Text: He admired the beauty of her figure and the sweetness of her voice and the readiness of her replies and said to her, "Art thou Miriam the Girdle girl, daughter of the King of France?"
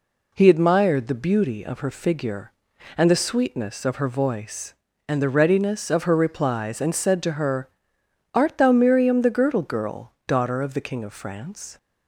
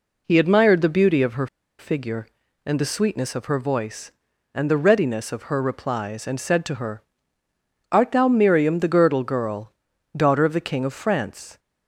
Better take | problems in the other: first | pauses between "her" and "figure"; slight; at 1.4 s; 0.32 s long

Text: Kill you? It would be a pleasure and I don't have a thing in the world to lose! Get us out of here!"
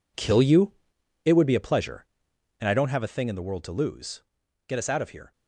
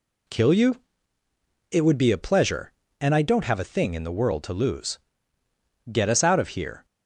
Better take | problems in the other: second | gets quieter; strong; throughout; 12 dB

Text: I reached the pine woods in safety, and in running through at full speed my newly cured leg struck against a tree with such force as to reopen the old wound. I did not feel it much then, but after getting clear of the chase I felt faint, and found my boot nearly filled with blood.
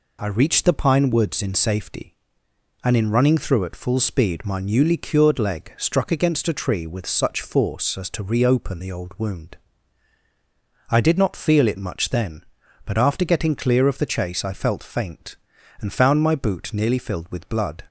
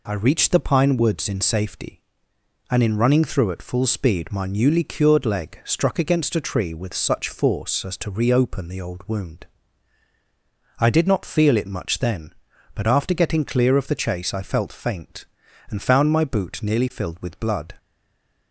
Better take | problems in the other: first | stays silent after the last word; slight; from 17.7 s on; 0.8 s long

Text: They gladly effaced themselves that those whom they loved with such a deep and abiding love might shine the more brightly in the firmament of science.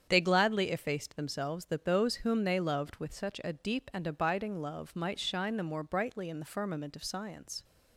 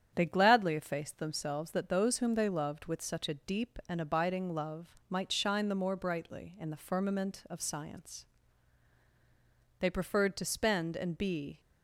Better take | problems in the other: first | starts louder than the rest; strong; until 1.1 s; 8.5 dB; strong in the first // goes on to say "They preferred to spend and be"; strong; from 9.7 s on; 1.8 s long

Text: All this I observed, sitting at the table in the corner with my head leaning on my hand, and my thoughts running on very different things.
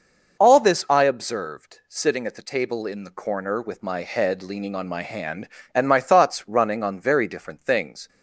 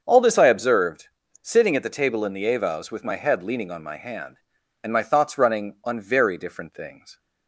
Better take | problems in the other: first | starts louder than the rest; until 1.0 s; 6.5 dB // says "avows" for "corner"; at 2.5 s

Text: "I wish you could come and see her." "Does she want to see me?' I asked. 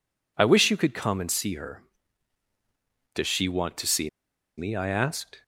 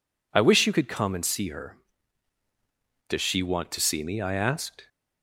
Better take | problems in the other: second | pauses between "see" and "me"; noticeable; at 4.0 s; 0.49 s long

